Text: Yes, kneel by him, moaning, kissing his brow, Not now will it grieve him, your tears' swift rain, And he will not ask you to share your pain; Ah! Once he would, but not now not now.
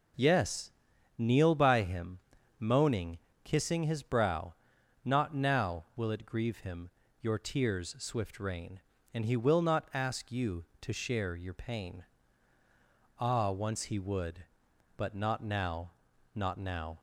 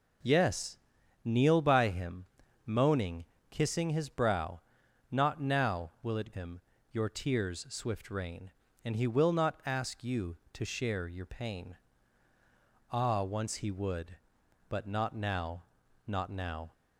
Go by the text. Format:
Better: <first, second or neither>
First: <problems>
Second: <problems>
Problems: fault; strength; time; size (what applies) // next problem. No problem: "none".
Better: first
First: pauses between "now" and "not"; noticeable; at 15.8 s; 0.46 s long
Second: skips "grieve"; at 6.3 s // pauses between "now" and "not"; noticeable; at 15.6 s; 0.46 s long